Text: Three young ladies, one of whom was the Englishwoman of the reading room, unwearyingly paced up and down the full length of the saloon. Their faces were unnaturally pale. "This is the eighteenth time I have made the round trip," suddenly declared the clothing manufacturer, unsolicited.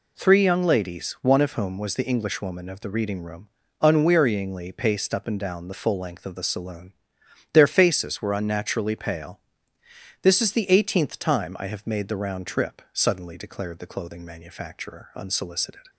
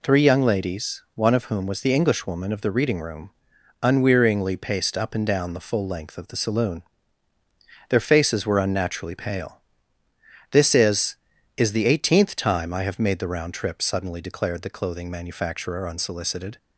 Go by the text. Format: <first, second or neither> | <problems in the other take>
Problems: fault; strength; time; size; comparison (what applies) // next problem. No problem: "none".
first | says "is" twice; at 11.5 s